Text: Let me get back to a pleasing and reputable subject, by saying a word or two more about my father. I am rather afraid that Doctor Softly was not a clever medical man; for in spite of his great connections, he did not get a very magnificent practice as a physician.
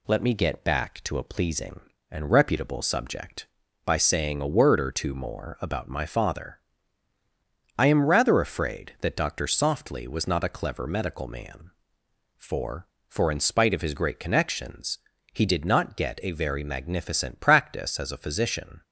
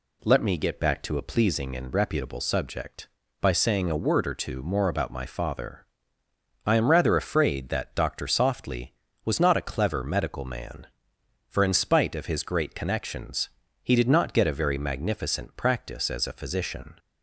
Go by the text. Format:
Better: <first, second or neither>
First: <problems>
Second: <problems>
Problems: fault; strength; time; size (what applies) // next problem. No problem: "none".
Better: second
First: says "for" twice; at 13.0 s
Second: none